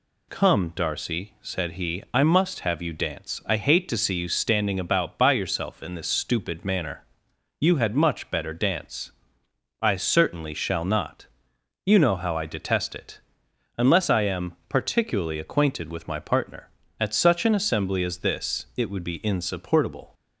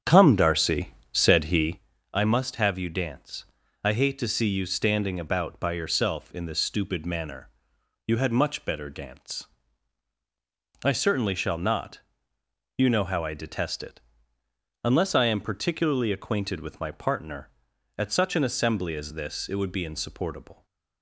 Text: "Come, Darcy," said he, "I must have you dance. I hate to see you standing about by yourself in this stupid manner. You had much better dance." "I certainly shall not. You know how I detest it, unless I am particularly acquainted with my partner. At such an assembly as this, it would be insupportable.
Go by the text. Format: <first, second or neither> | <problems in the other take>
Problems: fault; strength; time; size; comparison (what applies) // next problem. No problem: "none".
first | starts louder than the rest; strong; until 1.9 s; 8 dB